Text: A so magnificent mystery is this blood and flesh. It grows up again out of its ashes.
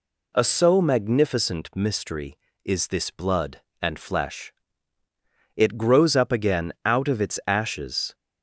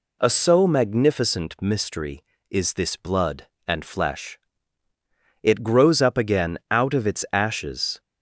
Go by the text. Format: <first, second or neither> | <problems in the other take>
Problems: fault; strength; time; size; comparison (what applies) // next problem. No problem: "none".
neither | none